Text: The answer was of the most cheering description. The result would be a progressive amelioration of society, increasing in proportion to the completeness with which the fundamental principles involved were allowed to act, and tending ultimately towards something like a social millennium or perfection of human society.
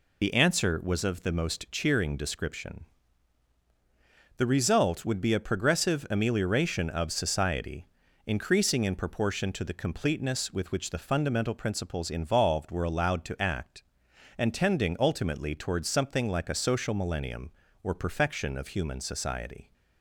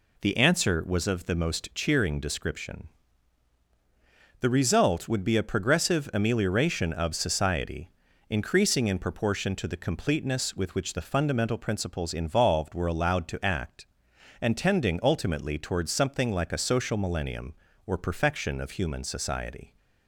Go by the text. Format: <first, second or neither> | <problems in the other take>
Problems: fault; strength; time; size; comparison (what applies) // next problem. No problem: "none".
second | loses the start of "The"; at 0.2 s; 75 ms